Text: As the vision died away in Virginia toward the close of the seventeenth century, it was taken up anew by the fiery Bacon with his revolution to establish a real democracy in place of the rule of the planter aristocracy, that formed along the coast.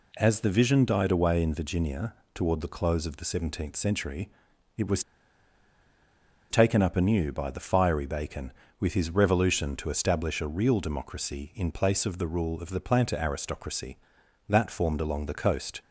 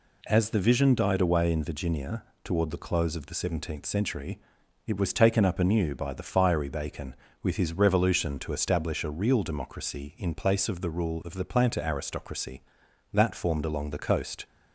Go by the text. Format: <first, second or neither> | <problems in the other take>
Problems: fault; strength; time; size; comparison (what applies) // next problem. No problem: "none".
second | pauses between "Virginia" and "toward"; slight; at 2.1 s; 0.20 s long; slight in the second // pauses between "was" and "taken"; strong; at 5.0 s; 1.4 s long